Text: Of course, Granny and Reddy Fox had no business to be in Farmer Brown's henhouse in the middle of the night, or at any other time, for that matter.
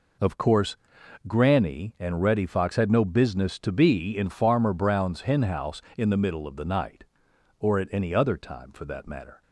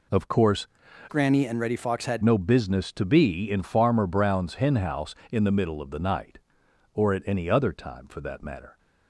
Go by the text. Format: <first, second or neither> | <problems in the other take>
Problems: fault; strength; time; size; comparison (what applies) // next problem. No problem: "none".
first | changes voice from "Granny" to "had"; from 1.0 to 2.2 s; 1.2 s long